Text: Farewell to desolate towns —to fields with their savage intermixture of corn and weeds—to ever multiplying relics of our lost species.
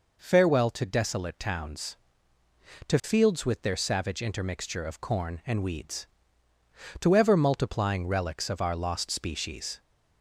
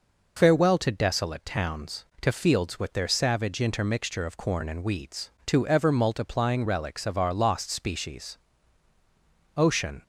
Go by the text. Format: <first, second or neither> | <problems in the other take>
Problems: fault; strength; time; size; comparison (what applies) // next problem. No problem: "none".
first | goes on to say "Ocean"; slight; from 9.5 s on; 0.46 s long